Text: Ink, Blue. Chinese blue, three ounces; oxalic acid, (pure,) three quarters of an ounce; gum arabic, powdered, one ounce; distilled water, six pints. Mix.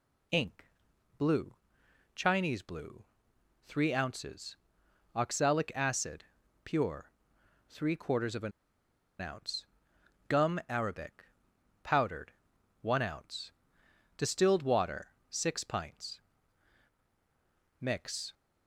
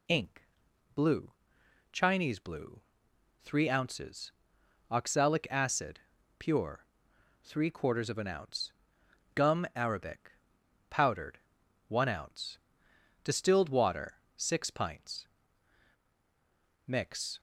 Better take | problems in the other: second | pauses between "an" and "ounce"; noticeable; at 8.5 s; 0.70 s long

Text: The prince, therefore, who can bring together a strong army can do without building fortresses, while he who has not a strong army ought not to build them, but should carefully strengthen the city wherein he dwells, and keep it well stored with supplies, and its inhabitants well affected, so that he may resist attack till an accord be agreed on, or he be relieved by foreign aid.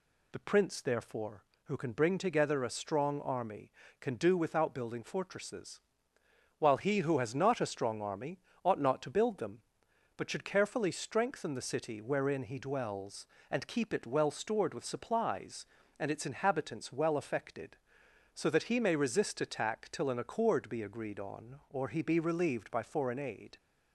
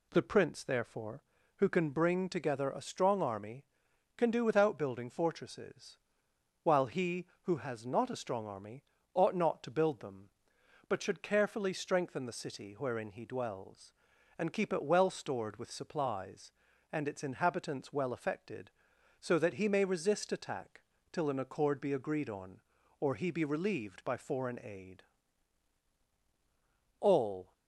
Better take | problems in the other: first | pauses between "army" and "ought"; slight; at 8.8 s; 0.30 s long; slight in the first // pauses between "attack" and "till"; slight; at 20.8 s; 0.32 s long // goes on to say "All"; from 26.9 s on; 0.54 s long

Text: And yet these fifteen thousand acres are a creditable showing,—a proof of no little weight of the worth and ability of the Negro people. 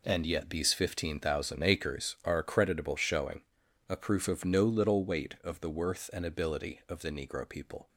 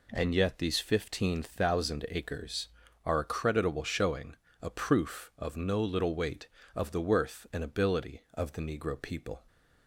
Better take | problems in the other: neither | none

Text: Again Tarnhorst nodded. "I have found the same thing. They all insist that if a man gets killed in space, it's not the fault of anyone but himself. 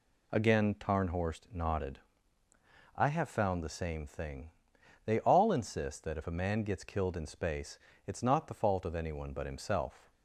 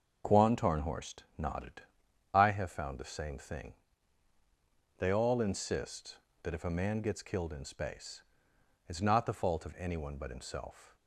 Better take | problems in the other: first | starts louder than the rest; until 1.4 s; 6.5 dB // says "Quan" for "Again"; at 0.2 s // pauses between "Tarnhorst" and "nodded"; slight; at 1.2 s; 0.16 s long

